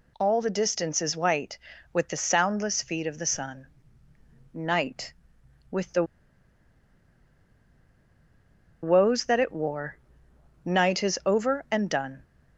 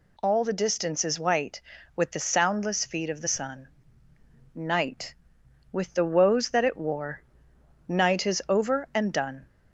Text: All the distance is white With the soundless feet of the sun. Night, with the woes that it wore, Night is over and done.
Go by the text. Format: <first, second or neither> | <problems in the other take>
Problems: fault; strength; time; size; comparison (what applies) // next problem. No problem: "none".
second | pauses between "the" and "woes"; strong; at 6.0 s; 2.7 s long